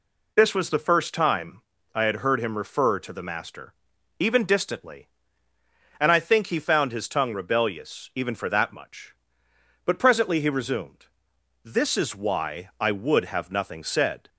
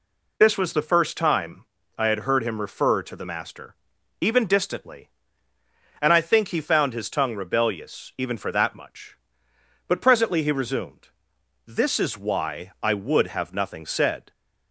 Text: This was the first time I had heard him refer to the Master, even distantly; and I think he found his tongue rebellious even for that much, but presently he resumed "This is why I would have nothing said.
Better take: neither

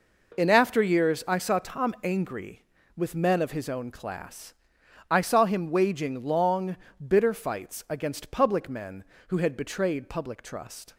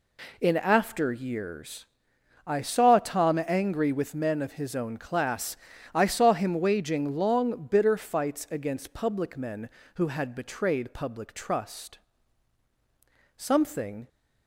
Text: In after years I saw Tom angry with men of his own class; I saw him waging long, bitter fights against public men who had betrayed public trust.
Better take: first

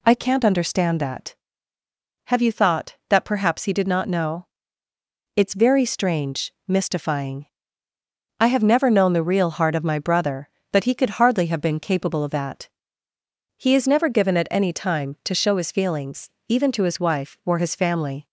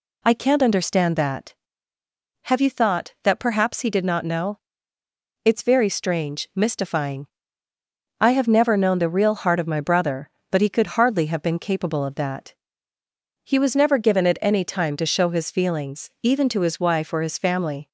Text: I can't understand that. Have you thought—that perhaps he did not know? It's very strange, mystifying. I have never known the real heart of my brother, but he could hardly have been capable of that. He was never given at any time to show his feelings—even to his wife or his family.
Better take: second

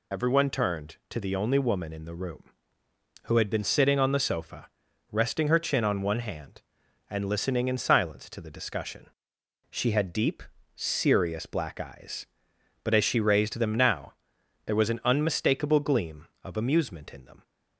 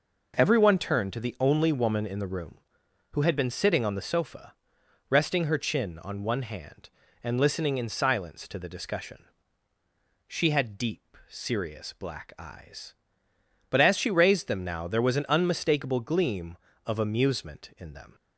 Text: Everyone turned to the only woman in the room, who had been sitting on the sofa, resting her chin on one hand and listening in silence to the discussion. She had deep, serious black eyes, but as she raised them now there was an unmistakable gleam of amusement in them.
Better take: second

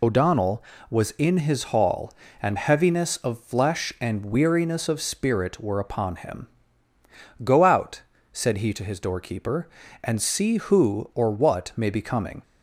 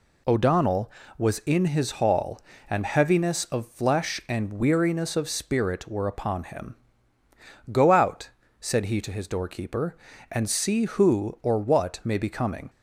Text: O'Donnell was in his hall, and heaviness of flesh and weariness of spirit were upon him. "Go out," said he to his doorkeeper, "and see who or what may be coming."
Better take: second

